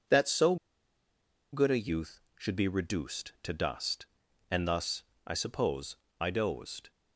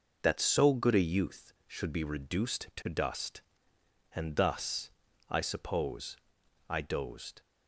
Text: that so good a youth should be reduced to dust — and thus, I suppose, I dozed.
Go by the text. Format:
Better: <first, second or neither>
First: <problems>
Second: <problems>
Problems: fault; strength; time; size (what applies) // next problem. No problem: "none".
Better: second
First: pauses between "so" and "good"; noticeable; at 0.5 s; 0.97 s long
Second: none